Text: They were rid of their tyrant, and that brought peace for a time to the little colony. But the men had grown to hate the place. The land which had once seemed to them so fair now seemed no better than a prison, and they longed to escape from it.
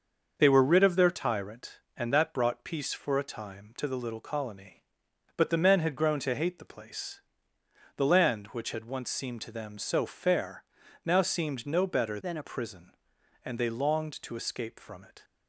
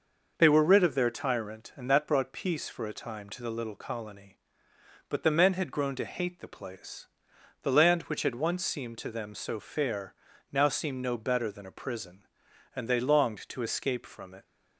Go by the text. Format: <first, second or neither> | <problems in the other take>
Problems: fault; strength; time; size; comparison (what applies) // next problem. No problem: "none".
second | starts louder than the rest; until 1.3 s; 6 dB // pauses between "fair" and "now"; at 10.6 s; 0.42 s long; also in the second // changes voice from "than" to "a"; from 12.2 to 12.4 s; 0.2 s long